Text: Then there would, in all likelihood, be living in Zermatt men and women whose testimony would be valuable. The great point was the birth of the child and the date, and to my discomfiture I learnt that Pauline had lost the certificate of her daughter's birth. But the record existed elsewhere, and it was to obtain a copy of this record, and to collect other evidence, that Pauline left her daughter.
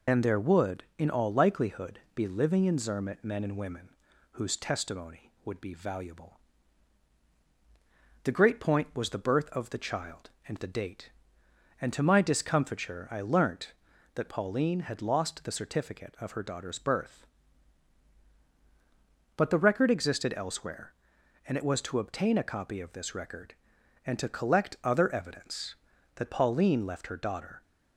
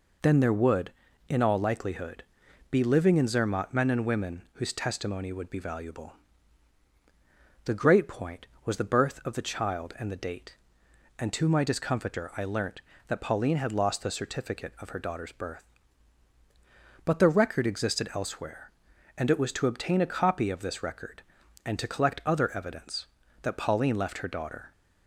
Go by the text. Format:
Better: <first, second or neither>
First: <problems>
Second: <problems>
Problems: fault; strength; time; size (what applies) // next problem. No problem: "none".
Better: second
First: loses the start of "Then"; at 0.0 s; 65 ms // pauses between "women" and "whose"; at 3.8 s; 0.42 s long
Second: none